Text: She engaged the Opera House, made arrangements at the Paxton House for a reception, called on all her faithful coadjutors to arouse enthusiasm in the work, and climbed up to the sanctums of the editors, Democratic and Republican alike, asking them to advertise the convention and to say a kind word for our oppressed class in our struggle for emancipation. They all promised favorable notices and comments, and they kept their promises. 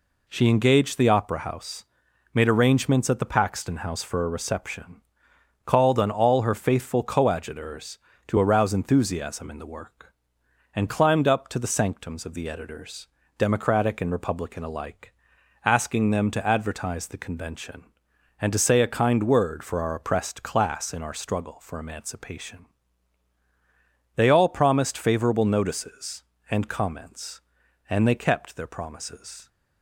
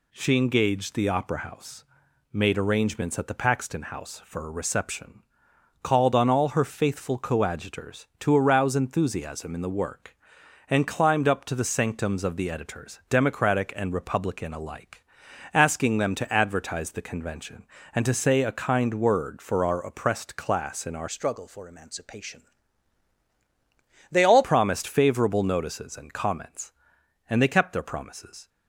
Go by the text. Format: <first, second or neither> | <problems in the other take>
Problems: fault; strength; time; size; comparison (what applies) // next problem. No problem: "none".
first | changes voice from "struggle" to "all"; from 21.0 to 24.4 s; 3.4 s long